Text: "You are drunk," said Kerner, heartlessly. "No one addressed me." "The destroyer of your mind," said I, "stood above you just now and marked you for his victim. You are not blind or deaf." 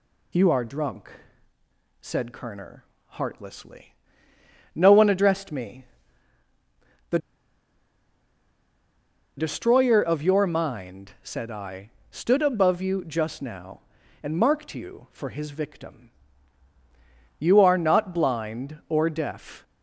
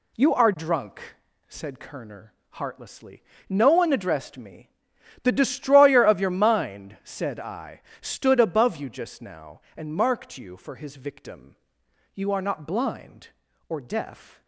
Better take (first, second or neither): second